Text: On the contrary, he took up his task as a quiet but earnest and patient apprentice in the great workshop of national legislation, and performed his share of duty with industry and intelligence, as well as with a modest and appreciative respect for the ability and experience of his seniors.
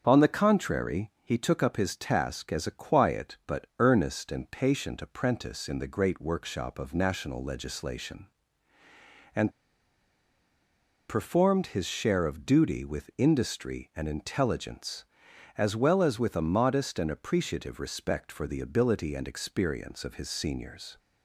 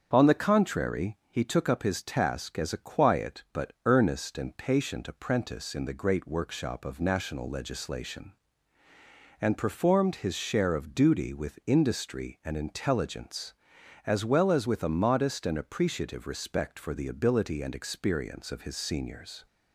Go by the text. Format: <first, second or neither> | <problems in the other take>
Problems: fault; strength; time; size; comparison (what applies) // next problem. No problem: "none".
second | starts louder than the rest; strong; until 1.0 s; 7 dB; strong in the second // pauses between "and" and "performed"; strong; at 9.5 s; 1.5 s long